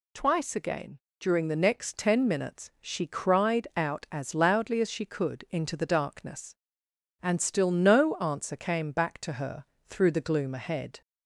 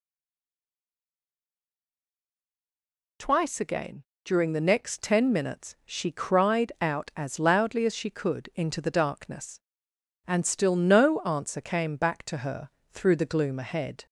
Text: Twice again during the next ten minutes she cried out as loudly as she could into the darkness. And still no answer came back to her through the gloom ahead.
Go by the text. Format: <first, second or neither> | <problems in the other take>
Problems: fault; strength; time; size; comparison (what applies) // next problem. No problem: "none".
first | stays silent before the first word; strong; until 3.1 s; 3.1 s long // pauses between "again" and "during"; slight; at 4.0 s; 0.20 s long; slight in the first // pauses between "her" and "through"; slight; at 12.6 s; 0.22 s long; slight in the first